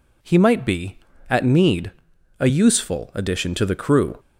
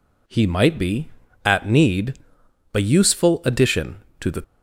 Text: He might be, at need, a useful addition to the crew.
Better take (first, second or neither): first